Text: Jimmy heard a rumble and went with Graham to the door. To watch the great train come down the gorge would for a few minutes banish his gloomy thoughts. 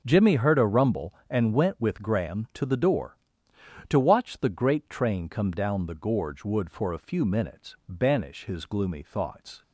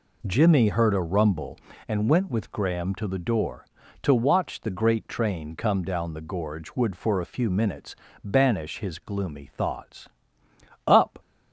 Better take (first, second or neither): first